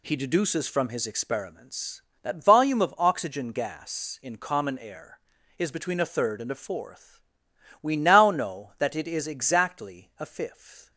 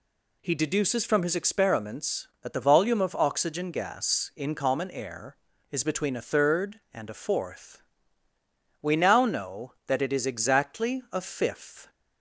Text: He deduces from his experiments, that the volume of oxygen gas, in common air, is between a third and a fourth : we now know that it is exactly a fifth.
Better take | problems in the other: second | skips "the"; at 2.4 s

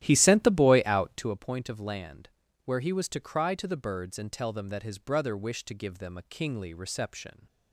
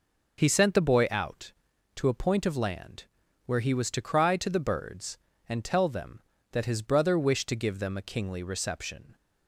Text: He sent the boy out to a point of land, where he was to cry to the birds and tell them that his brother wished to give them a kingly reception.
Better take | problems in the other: second | starts louder than the rest; strong; until 1.4 s; 13.5 dB

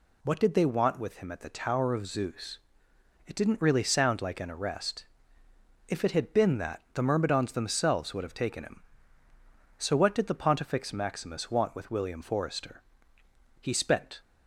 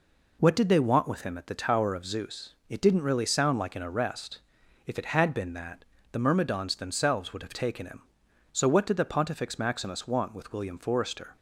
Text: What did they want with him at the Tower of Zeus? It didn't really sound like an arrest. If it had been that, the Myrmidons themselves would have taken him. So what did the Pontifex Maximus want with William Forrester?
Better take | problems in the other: second | goes on to say "He spent"; from 13.6 s on; 0.58 s long

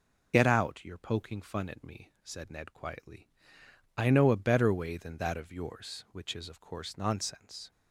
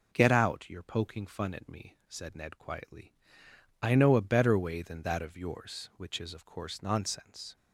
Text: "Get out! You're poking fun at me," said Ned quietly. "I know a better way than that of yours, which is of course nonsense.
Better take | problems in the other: second | loses the start of "Get"; at 0.3 s; 50 ms

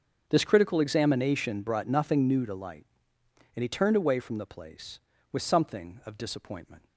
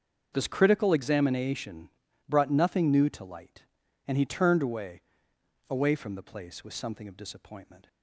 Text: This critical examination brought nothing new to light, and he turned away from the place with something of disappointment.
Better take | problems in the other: first | starts louder than the rest; until 1.3 s; 6.5 dB; also in the first // pauses between "examination" and "brought"; at 1.8 s; 0.38 s long // says "away" twice; at 5.6 s

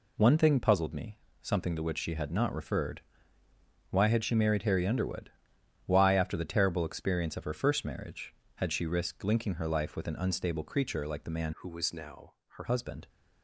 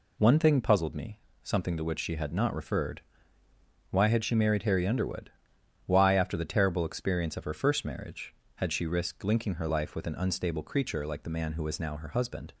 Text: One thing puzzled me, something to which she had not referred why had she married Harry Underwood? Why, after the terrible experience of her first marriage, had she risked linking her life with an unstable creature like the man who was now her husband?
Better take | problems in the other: second | pauses between "referred" and "why"; noticeable; at 3.0 s; 0.88 s long; noticeable in the second // changes voice from "who" to "her"; from 11.5 to 12.6 s; 1.1 s long // pauses between "now" and "her"; slight; at 12.3 s; 0.24 s long

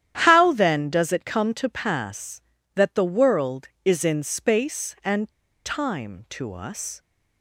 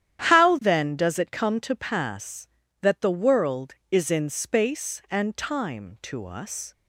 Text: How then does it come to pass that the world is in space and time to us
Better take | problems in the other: second | starts louder than the rest; strong; until 1.2 s; 10.5 dB; strong in the second // pauses between "and" and "time"; slight; at 5.2 s; 0.35 s long

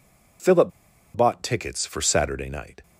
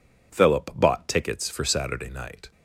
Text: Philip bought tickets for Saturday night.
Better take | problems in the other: second | pauses between "Philip" and "bought"; at 0.7 s; 0.45 s long

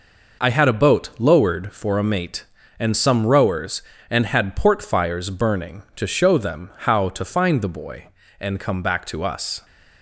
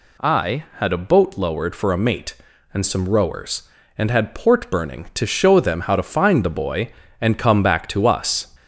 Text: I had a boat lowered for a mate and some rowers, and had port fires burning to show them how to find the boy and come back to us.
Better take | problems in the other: first | skips "fires"; at 4.6 s

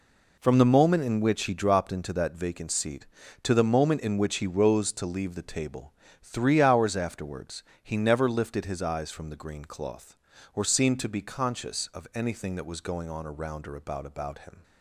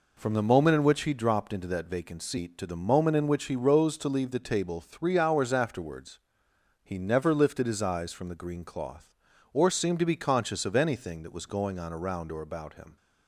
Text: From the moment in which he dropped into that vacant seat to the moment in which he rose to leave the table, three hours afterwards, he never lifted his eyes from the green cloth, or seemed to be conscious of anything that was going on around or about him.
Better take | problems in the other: second | says "about" twice; at 14.0 s

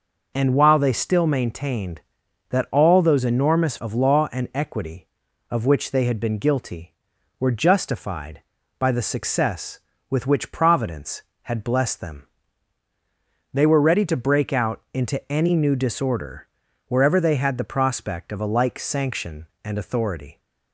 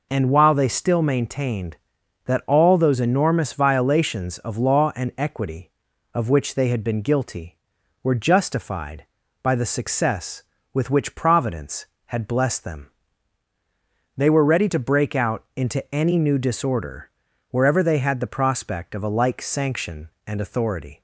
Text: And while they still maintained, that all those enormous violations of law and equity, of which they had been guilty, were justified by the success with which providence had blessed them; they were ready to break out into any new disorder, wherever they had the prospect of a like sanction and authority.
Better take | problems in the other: second | skips "violations"; at 3.7 s

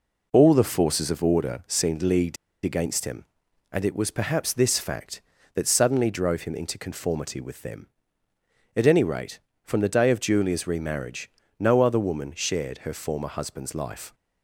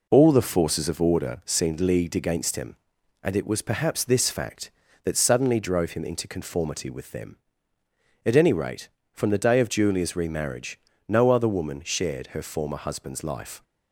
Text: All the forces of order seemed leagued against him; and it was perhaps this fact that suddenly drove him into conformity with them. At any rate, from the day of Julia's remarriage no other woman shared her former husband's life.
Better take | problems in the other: second | pauses between "leagued" and "against"; slight; at 2.3 s; 0.28 s long // pauses between "remarriage" and "no"; slight; at 11.2 s; 0.30 s long; slight in the second

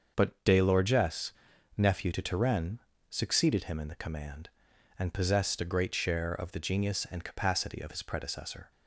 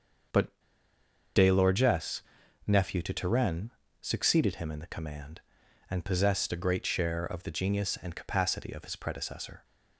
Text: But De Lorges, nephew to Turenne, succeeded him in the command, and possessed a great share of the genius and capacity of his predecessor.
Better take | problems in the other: first | starts louder than the rest; until 2.1 s; 6.5 dB; also in the first // pauses between "But" and "De"; noticeable; at 0.4 s; 0.86 s long

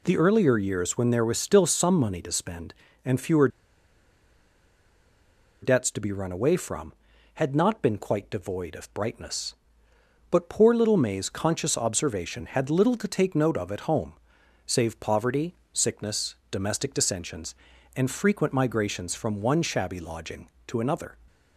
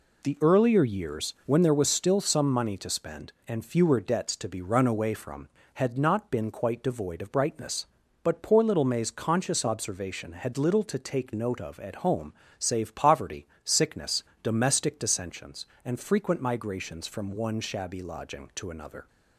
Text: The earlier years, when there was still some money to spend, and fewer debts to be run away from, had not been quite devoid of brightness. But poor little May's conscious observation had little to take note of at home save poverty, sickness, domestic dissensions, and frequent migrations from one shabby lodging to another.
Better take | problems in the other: second | pauses between "fewer" and "debts"; strong; at 3.4 s; 2.1 s long // pauses between "home" and "save"; noticeable; at 14.1 s; 0.54 s long; slight in the second

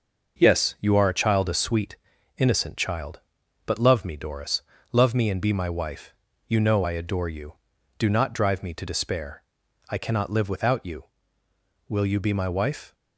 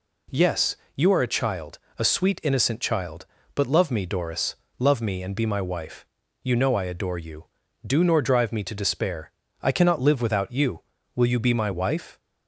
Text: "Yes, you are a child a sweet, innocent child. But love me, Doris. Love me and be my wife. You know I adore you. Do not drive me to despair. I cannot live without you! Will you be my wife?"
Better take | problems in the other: first | pauses between "child" and "a"; slight; at 1.7 s; 0.18 s long // says "nor" for "not"; at 8.0 s

